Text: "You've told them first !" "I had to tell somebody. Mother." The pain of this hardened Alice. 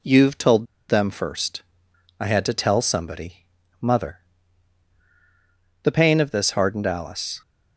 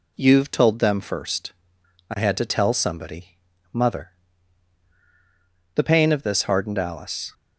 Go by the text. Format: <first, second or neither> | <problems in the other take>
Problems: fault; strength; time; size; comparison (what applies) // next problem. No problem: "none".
second | pauses between "told" and "them"; slight; at 0.6 s; 0.24 s long